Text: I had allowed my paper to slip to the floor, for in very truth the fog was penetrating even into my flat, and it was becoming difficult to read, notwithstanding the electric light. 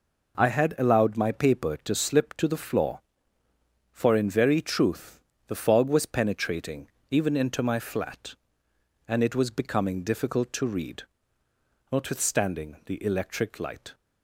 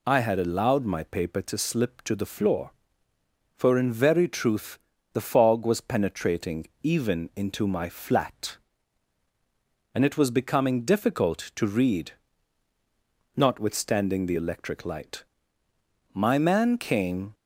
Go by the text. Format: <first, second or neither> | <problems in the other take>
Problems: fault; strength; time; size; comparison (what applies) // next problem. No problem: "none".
first | pauses between "truth" and "the"; slight; at 4.7 s; 0.34 s long; slight in the first // pauses between "penetrating" and "even"; slight; at 6.6 s; 0.16 s long; slight in the first // goes on to say "My man came"; noticeable; from 16.1 s on; 1.2 s long